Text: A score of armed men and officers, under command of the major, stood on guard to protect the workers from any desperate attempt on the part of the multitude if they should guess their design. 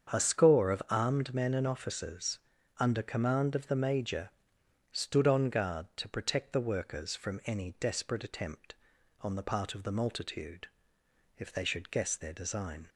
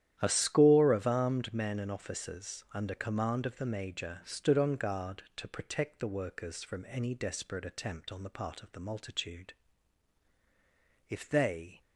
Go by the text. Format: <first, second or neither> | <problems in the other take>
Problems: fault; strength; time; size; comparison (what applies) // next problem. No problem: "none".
first | starts louder than the rest; strong; until 1.2 s; 11 dB; strong in the first // pauses between "multitude" and "if"; strong; at 9.5 s; 1.5 s long; noticeable in the first // stops before "should guess their design"; at 11.8 s